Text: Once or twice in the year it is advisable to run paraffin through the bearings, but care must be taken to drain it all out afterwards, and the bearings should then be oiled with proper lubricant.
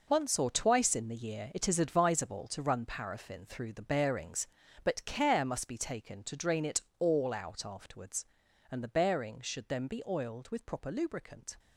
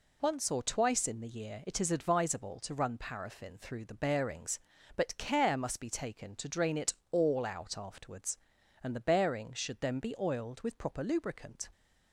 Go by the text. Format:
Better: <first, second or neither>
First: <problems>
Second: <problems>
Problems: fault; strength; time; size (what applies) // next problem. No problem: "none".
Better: second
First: gets quieter; strong; throughout; 11 dB // pauses between "it" and "all"; slight; at 6.8 s; 0.18 s long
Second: pauses between "it" and "all"; slight; at 6.9 s; 0.18 s long